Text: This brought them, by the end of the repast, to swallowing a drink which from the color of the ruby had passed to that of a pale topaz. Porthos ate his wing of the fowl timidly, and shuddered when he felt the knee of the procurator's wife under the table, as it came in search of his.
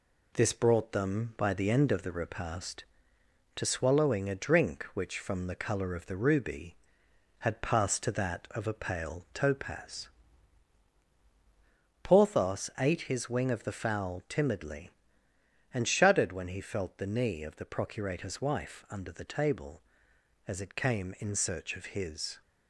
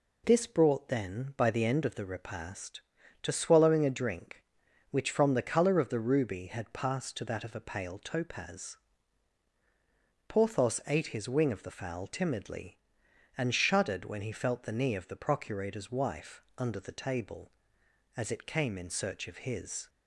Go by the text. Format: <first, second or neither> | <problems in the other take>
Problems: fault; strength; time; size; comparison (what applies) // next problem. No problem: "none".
first | says "then" for "them"; at 0.8 s // pauses between "wife" and "under"; slight; at 16.4 s; 0.16 s long